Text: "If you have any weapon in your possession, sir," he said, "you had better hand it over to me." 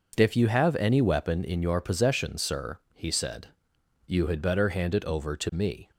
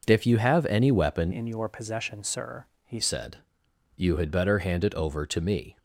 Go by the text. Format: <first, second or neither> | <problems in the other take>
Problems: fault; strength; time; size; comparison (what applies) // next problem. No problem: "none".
first | changes voice from "in" to "he"; from 1.3 to 3.0 s; 1.7 s long